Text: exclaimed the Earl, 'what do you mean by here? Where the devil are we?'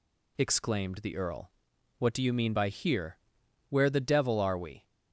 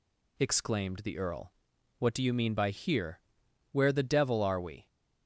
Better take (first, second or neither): neither